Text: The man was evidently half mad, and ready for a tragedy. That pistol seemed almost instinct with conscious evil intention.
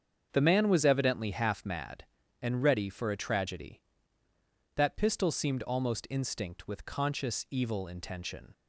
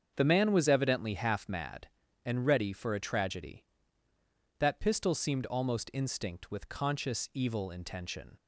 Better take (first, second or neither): neither